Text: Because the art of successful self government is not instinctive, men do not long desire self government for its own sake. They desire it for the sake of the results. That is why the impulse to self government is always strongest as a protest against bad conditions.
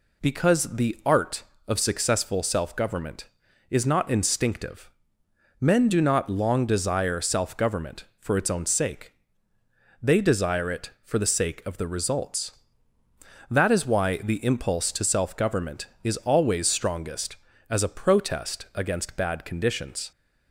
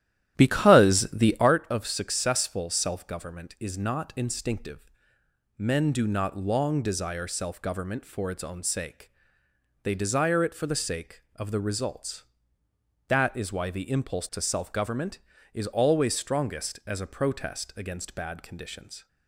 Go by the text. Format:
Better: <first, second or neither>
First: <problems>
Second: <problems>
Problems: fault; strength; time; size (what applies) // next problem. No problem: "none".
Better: first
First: none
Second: starts louder than the rest; strong; until 1.5 s; 12 dB